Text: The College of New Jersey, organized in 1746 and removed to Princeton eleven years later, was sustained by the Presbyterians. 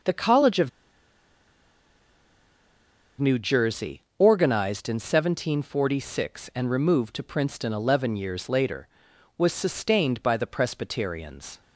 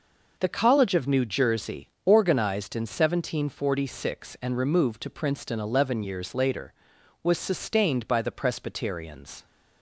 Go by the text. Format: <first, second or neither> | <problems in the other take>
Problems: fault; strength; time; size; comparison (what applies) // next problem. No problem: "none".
second | pauses between "of" and "New"; strong; at 0.6 s; 2.5 s long